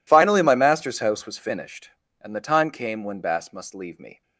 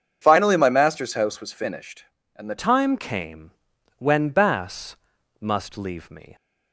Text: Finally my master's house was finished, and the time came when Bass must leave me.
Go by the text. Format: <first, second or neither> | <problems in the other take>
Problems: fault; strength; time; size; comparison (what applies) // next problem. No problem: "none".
first | changes voice at "time"; from 2.5 s on; 3.8 s long // pauses between "came" and "when"; noticeable; at 3.5 s; 0.46 s long // pauses between "Bass" and "must"; at 4.9 s; 0.42 s long